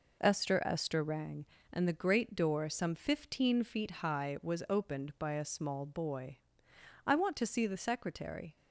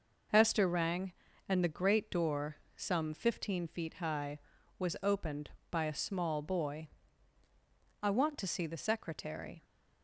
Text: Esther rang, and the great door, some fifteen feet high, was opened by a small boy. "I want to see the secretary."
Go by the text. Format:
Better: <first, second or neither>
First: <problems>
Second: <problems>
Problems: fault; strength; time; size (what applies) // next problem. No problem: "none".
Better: second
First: says "Esther" twice; at 0.6 s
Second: none